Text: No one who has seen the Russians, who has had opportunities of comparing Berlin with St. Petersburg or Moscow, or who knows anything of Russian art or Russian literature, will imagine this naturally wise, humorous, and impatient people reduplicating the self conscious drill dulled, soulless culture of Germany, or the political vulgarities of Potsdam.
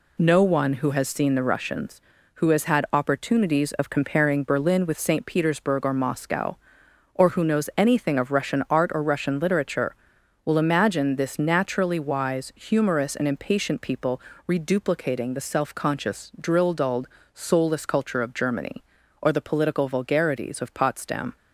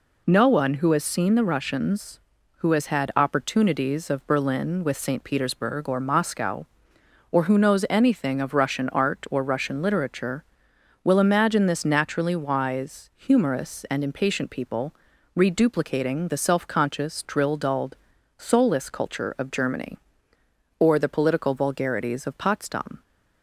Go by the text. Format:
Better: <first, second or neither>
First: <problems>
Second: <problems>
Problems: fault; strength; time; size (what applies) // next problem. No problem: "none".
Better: first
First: pauses between "people" and "reduplicating"; slight; at 14.1 s; 0.28 s long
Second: skips "comparing"; at 4.2 s // pauses between "people" and "reduplicating"; at 14.9 s; 0.40 s long